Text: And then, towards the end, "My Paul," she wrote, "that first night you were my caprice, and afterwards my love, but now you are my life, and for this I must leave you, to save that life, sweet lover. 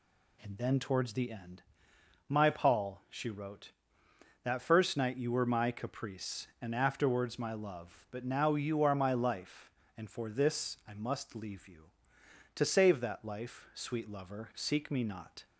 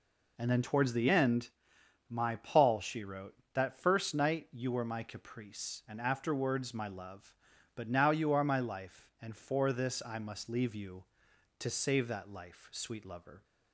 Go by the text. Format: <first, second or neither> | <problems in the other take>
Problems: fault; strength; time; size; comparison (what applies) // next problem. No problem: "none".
second | goes on to say "Seek me not"; noticeable; from 14.5 s on; 0.90 s long